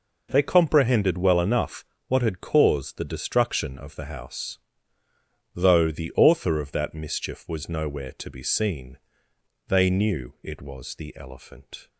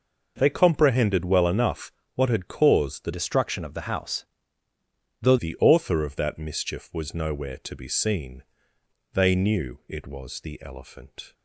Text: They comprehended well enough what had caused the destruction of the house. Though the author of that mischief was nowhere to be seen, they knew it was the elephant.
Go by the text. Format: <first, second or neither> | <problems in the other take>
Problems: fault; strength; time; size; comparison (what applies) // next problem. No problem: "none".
first | pauses between "enough" and "what"; slight; at 1.9 s; 0.24 s long; slight in the first // changes voice from "destruction" to "Though"; from 3.1 to 5.3 s; 2.2 s long